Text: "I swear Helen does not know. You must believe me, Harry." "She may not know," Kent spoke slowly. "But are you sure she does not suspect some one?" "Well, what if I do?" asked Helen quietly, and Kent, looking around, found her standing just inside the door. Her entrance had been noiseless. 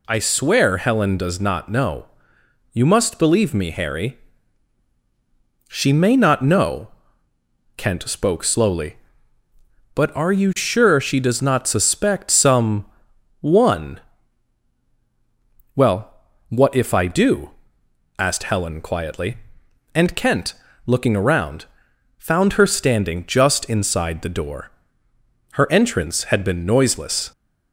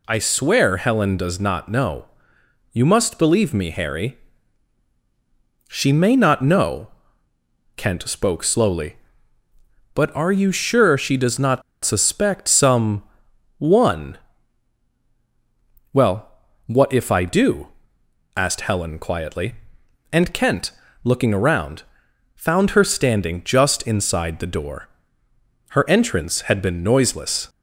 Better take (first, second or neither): first